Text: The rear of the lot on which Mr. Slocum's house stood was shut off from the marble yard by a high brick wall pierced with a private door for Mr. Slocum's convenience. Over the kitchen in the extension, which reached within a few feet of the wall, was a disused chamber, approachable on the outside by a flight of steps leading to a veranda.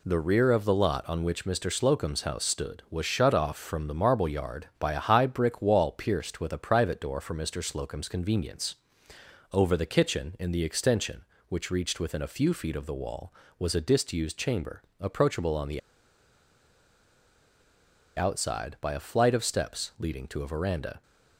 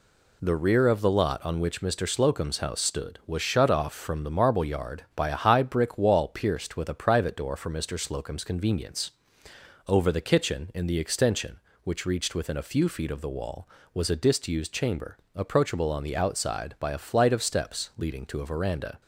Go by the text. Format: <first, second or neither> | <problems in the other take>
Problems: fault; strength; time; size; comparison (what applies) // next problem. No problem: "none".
second | pauses between "the" and "outside"; strong; at 15.7 s; 2.3 s long